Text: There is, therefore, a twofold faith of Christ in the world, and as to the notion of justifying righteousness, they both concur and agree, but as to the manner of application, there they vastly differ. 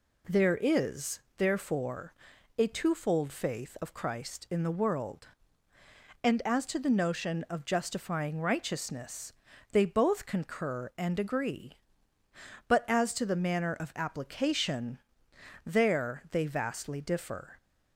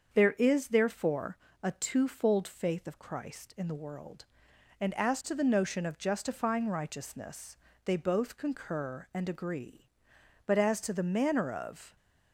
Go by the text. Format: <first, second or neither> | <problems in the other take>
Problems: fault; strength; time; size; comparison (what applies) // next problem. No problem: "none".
first | starts louder than the rest; until 1.1 s; 7 dB // stops before "application there they vastly differ"; at 11.9 s